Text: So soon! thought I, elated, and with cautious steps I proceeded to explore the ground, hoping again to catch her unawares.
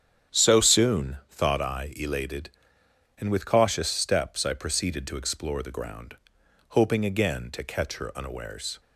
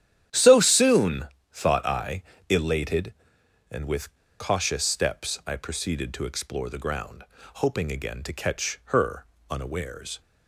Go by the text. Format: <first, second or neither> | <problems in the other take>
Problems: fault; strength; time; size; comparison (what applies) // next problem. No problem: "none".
first | starts louder than the rest; strong; until 1.5 s; 10.5 dB; strong in the first // pauses between "with" and "cautious"; slight; at 4.1 s; 0.25 s long // pauses between "her" and "unawares"; slight; at 9.2 s; 0.26 s long